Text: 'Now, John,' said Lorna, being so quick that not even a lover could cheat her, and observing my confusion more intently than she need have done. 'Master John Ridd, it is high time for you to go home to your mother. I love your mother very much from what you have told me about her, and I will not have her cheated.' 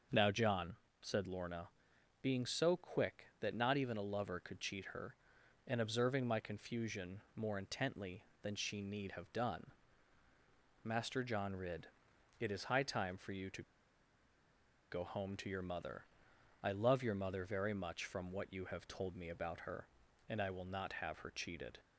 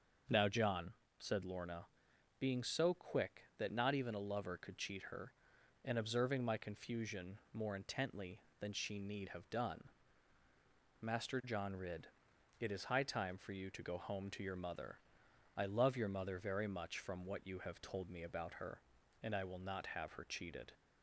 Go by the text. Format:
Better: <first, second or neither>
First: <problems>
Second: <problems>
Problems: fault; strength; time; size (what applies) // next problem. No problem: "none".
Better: second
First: starts louder than the rest; until 1.3 s; 6.5 dB // pauses between "to" and "go"; strong; at 13.6 s; 1.2 s long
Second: starts louder than the rest; until 1.5 s; 6 dB